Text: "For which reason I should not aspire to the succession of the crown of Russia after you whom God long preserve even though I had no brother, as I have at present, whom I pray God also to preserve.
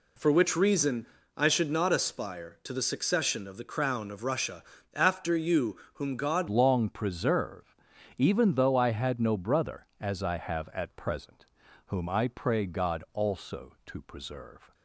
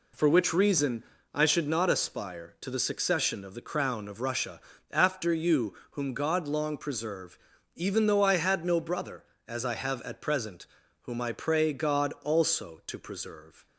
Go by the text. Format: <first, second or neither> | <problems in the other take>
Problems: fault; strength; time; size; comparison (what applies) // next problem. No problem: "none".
second | pauses between "reason" and "I"; slight; at 1.0 s; 0.30 s long; slight in the second // pauses between "Russia" and "after"; slight; at 4.6 s; 0.32 s long; slight in the second // pauses between "you" and "whom"; slight; at 5.7 s; 0.16 s long; slight in the second // changes voice at "long"; from 6.4 s on; 8.3 s long // pauses between "preserve" and "even"; at 7.7 s; 0.44 s long; also in the second